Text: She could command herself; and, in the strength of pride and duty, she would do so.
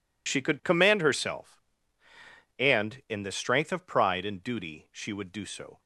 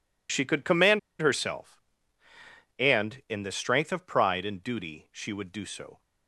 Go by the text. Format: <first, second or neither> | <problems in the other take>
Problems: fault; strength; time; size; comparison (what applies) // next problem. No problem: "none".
first | pauses between "command" and "herself"; slight; at 0.9 s; 0.20 s long